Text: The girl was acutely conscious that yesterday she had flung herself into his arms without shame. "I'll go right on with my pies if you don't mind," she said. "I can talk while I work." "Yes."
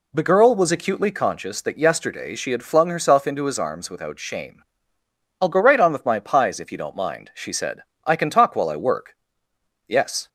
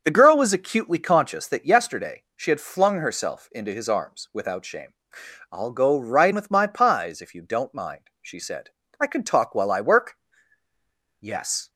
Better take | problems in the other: first | starts louder than the rest; until 1.0 s; 6.5 dB // skips "on"; at 6.3 s

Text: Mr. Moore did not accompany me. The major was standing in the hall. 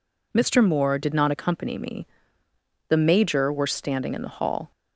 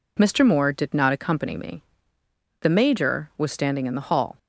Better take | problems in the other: second | says "were" for "was"; at 3.5 s

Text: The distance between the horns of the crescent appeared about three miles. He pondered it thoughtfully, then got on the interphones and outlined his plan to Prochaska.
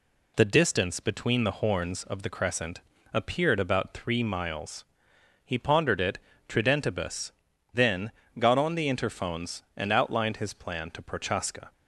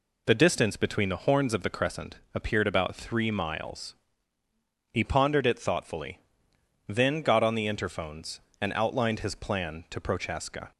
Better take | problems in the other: second | pauses between "crescent" and "appeared"; slight; at 2.8 s; 0.32 s long; slight in the second // says "tridentibus" for "thoughtfully"; at 6.4 s // pauses between "then" and "got"; slight; at 8.1 s; 0.28 s long

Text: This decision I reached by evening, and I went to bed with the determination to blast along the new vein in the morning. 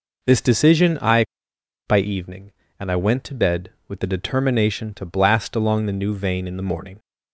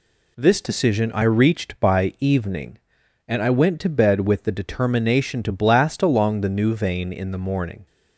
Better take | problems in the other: second | skips "reached"; at 1.5 s

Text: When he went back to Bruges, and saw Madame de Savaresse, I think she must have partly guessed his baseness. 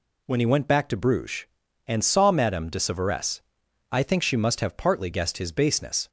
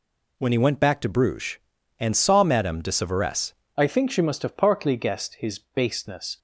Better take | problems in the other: first | changes voice at "I"; from 3.7 s on; 2.6 s long

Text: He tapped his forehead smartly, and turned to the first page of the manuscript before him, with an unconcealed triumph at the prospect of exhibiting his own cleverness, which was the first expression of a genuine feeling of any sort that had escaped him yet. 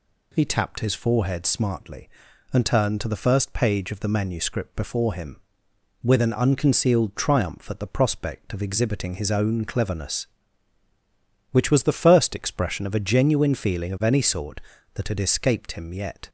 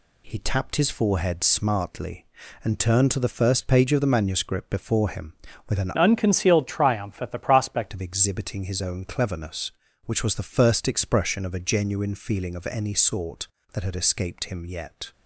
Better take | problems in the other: first | changes voice from "unconcealed" to "prospect"; from 5.9 to 7.8 s; 1.9 s long

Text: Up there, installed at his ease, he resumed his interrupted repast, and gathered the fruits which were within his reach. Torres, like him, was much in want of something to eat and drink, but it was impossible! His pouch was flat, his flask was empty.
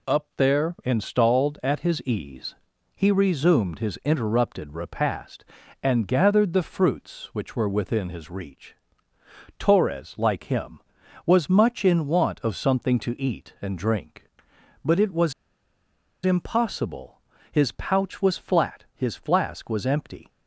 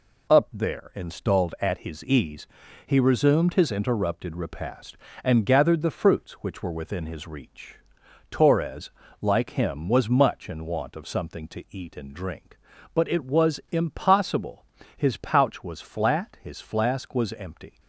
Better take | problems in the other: second | pauses between "was" and "impossible"; noticeable; at 15.3 s; 0.93 s long

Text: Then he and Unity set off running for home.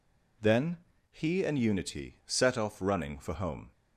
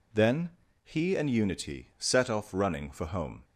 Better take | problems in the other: neither | pauses between "Then" and "he"; slight; the same in both

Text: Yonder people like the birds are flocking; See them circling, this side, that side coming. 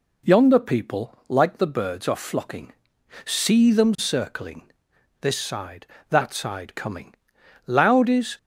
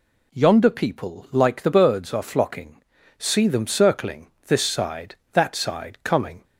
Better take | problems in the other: second | goes on to say "Loud is"; noticeable; from 7.6 s on; 0.72 s long

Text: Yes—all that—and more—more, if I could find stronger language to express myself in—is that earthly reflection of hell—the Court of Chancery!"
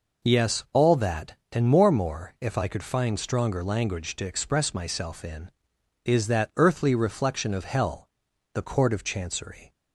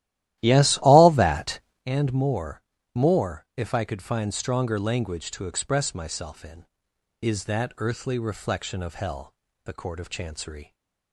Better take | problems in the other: first | starts louder than the rest; strong; until 1.9 s; 14 dB

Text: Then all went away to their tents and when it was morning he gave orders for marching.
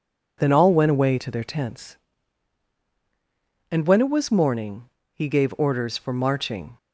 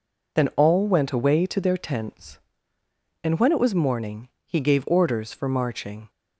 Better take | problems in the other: neither | pauses between "morning" and "he"; slight; the same in both

